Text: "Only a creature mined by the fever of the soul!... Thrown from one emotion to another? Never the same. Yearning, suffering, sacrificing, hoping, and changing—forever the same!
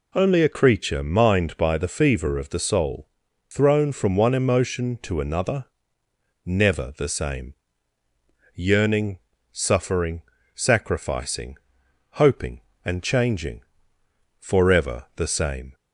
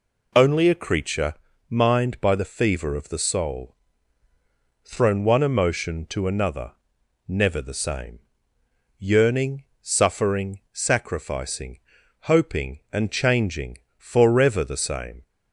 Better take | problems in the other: first | pauses between "creature" and "mined"; slight; at 1.3 s; 0.34 s long // skips "from"; at 5.2 s

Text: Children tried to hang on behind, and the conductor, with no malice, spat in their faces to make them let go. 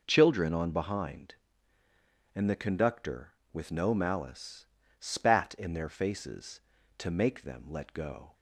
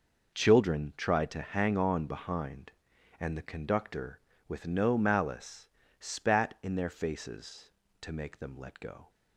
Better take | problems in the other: second | skips "tried to hang"; at 0.5 s

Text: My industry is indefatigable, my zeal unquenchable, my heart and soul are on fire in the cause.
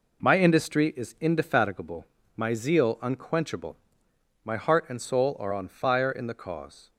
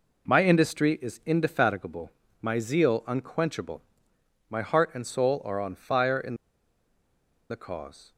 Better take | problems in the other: first | pauses between "in" and "the"; at 6.3 s; 1.1 s long

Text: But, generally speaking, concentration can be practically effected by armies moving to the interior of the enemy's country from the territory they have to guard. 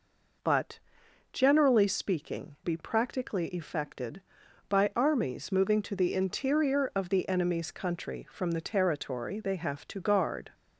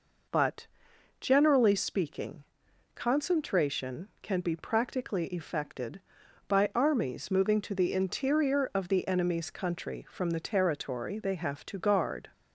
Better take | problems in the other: second | skips "concentration can"; at 2.5 s

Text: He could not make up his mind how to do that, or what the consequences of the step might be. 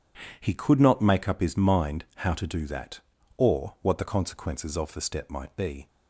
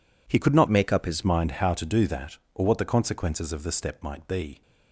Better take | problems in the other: first | changes voice from "make" to "his"; from 0.6 to 1.2 s; 0.6 s long

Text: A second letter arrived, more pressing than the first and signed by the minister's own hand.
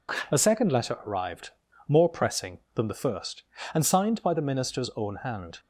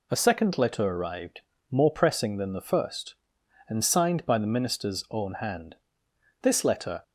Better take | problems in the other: first | goes on to say "This letter"; from 6.4 s on; 0.60 s long

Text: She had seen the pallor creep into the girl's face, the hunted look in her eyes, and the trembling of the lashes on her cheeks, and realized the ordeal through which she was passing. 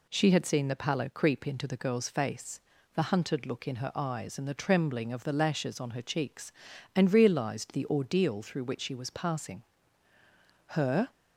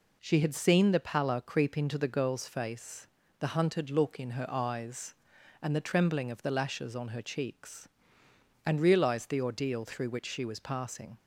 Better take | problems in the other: second | goes on to say "Her"; slight; from 10.6 s on; 0.42 s long

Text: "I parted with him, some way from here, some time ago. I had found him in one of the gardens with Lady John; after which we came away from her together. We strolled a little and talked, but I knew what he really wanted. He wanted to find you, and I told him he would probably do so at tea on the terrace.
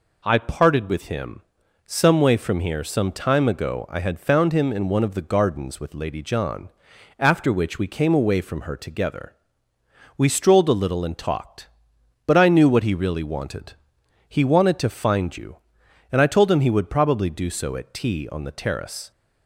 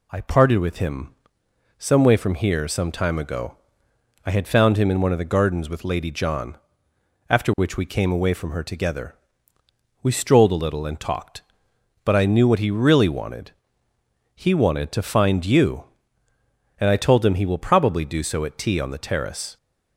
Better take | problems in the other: first | says "will" for "would"; at 17.4 s

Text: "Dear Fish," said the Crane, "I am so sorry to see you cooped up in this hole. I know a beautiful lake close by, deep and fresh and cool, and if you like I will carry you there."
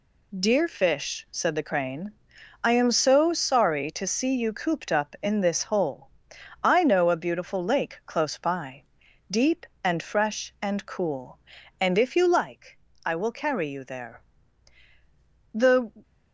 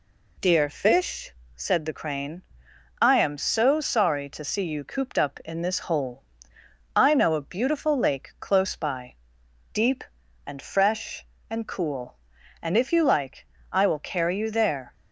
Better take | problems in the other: second | pauses between "like" and "I"; slight; at 12.7 s; 0.28 s long; slight in the second // goes on to say "The"; slight; from 15.5 s on; 0.38 s long

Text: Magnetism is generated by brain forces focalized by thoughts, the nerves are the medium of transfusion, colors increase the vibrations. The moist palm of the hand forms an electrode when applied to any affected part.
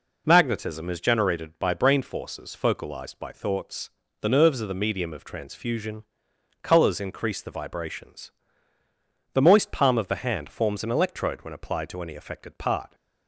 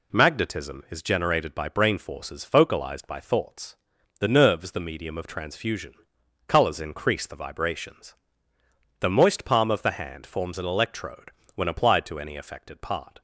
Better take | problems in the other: first | skips "are"; at 4.7 s // pauses between "electrode" and "when"; slight; at 11.3 s; 0.24 s long

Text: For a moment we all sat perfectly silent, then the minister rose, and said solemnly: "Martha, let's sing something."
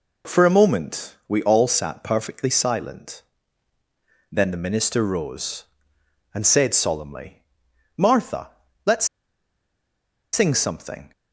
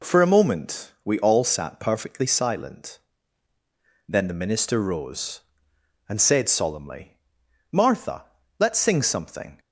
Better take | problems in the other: second | pauses between "let's" and "sing"; strong; at 9.0 s; 1.2 s long

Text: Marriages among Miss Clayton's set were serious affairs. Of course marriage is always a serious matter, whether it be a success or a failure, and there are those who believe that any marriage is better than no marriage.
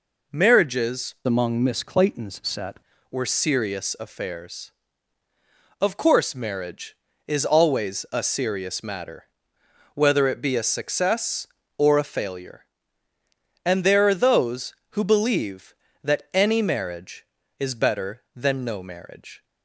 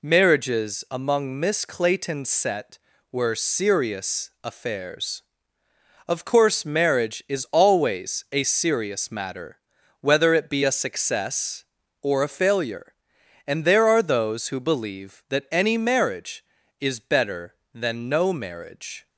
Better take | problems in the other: second | changes voice from "among" to "set"; from 1.2 to 2.7 s; 1.5 s long

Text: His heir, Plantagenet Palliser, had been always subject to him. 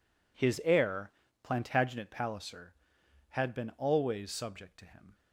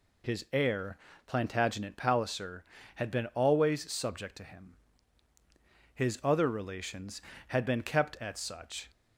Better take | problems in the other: first | goes on to say "His other relations had been kept at such"; strong; from 5.9 s on; 2.9 s long

